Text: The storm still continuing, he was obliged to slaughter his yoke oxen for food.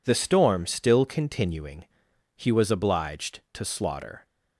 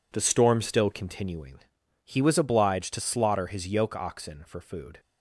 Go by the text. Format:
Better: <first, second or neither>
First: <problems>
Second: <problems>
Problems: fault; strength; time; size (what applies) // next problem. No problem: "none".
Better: second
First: stops before "his yoke oxen for food"; at 4.2 s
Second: none